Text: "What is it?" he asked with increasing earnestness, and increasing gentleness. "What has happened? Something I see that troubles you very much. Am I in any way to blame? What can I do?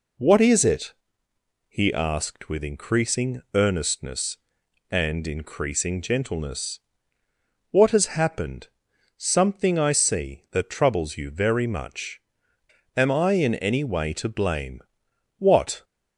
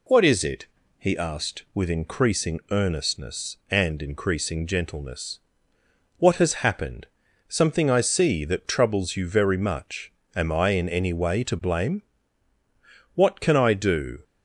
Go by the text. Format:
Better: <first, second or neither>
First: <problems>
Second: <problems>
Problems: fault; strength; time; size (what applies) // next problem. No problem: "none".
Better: second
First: stops before "can I do"; at 15.8 s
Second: none